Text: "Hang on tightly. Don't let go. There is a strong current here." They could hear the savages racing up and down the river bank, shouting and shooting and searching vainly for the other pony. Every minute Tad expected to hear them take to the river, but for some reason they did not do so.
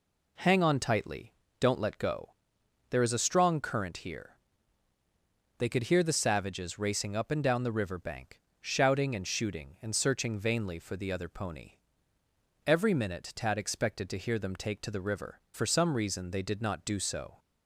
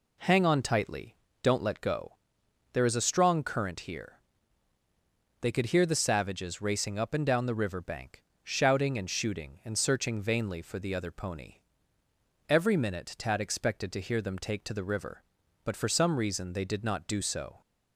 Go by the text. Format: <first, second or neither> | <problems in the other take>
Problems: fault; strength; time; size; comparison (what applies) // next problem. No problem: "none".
second | skips "but"; at 15.4 s